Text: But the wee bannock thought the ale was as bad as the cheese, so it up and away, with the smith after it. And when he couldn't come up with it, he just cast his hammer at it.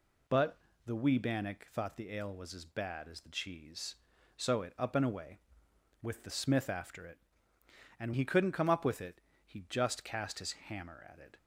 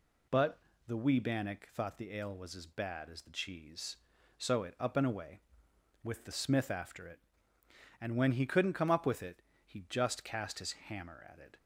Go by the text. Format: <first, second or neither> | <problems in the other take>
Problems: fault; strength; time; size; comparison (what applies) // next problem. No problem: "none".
second | pauses between "But" and "the"; slight; at 0.5 s; 0.28 s long; slight in the second // skips "when"; at 8.1 s